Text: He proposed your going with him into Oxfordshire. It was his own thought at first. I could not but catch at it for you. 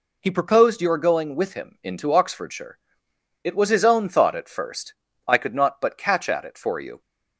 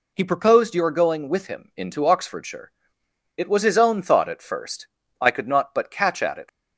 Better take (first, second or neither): first